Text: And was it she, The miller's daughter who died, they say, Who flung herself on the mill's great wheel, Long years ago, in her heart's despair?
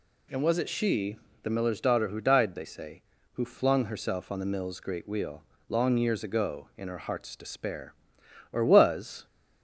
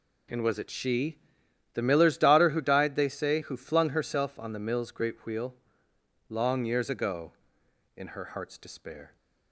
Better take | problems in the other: second | goes on to say "Or was"; noticeable; from 8.5 s on; 0.74 s long

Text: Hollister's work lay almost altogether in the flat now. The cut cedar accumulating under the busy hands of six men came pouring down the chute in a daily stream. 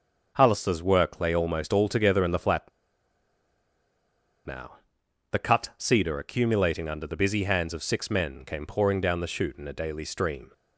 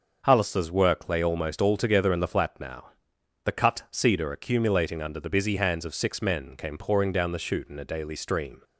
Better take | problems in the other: second | starts louder than the rest; noticeable; until 1.3 s; 6 dB; noticeable in the second // pauses between "flat" and "now"; strong; at 2.6 s; 1.7 s long

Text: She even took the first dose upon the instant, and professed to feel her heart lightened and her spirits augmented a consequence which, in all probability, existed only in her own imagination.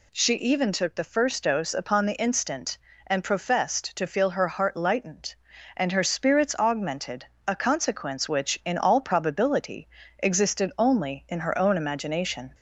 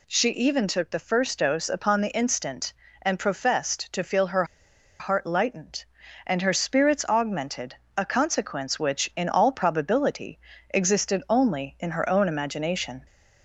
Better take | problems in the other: first | pauses between "her" and "heart"; noticeable; at 4.4 s; 0.55 s long // pauses between "augmented" and "a"; slight; at 7.7 s; 0.20 s long; slight in the first

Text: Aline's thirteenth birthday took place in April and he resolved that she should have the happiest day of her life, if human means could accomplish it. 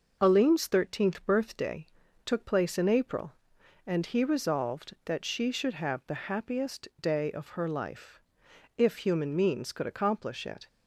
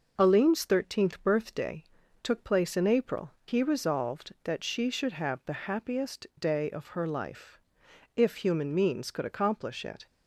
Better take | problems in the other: first | pauses between "birthday" and "took"; at 1.8 s; 0.38 s long; also in the first // skips "and"; at 3.3 s

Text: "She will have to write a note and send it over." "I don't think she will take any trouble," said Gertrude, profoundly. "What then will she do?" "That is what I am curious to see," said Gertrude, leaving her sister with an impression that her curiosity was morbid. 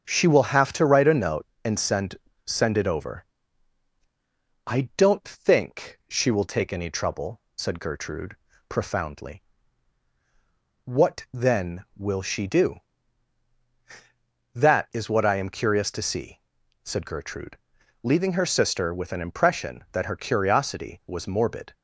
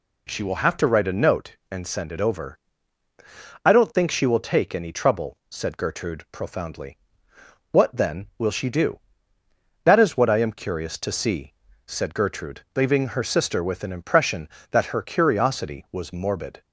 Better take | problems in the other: second | starts louder than the rest; until 1.0 s; 7 dB // says "send" twice; at 2.4 s

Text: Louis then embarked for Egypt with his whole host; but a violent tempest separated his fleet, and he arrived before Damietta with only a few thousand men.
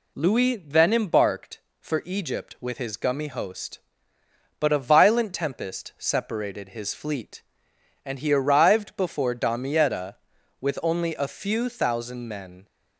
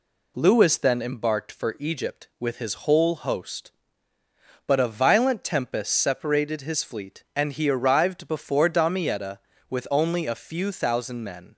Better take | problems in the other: second | says "gummy" for "whole"; at 2.9 s

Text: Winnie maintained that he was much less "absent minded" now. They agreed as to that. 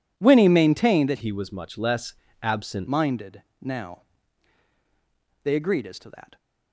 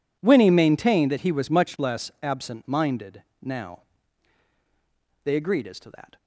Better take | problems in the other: second | changes voice from "he" to "absent"; from 1.2 to 2.8 s; 1.6 s long // pauses between "less" and "absent"; slight; at 2.1 s; 0.28 s long // pauses between "minded" and "now"; slight; at 3.4 s; 0.18 s long; slight in the second

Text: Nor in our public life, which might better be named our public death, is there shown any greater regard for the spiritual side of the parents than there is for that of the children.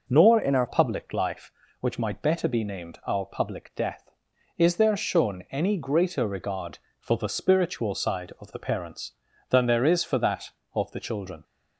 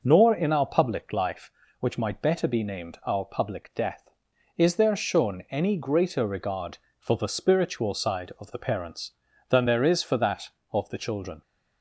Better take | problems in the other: second | changes voice from "in" to "our"; from 0.4 to 0.6 s; 0.2 s long

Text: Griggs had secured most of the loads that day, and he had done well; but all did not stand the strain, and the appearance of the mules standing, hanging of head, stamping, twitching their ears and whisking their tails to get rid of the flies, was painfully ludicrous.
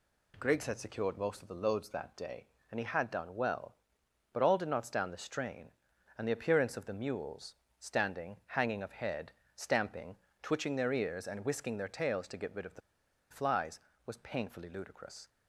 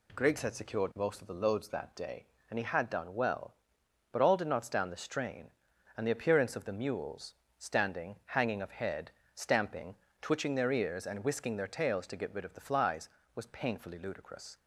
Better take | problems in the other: second | pauses between "mules" and "standing"; slight; at 7.5 s; 0.24 s long; slight in the second // pauses between "the" and "flies"; noticeable; at 12.8 s; 0.50 s long

